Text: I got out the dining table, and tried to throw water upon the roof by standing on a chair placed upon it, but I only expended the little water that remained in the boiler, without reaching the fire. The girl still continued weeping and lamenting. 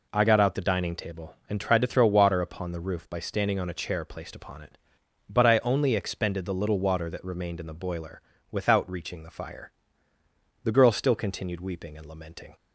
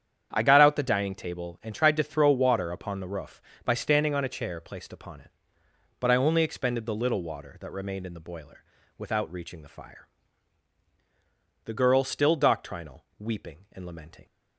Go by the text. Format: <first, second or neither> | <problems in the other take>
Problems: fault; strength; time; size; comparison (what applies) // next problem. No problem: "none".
first | starts louder than the rest; strong; until 1.3 s; 8.5 dB // says "doctrinal" for "continued"; at 12.3 s